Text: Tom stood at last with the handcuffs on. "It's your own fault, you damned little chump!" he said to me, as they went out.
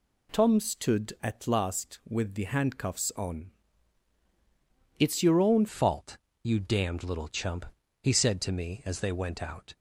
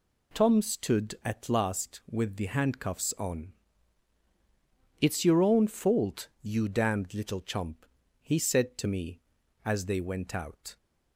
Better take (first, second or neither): second